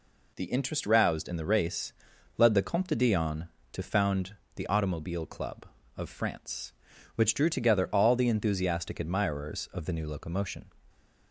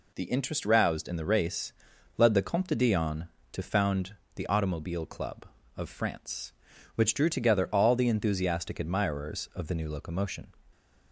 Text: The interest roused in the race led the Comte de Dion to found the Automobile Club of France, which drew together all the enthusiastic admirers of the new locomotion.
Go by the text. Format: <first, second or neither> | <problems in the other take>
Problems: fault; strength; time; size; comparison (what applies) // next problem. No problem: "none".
neither | pauses between "race" and "led"; the same in both // pauses between "found" and "the"; slight; the same in both